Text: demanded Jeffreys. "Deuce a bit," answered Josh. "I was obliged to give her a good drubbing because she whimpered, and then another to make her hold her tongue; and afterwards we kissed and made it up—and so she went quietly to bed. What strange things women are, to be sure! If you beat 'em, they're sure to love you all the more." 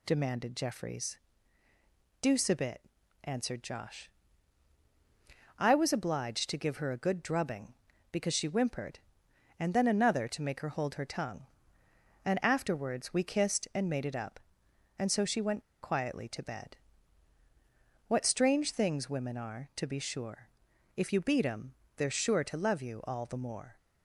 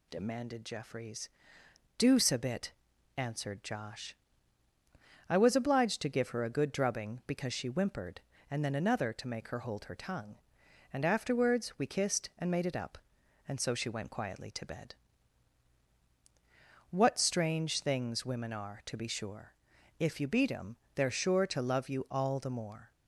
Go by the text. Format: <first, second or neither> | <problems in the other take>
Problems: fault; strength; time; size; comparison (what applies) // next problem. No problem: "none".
second | pauses between "went" and "quietly"; slight; at 15.6 s; 0.20 s long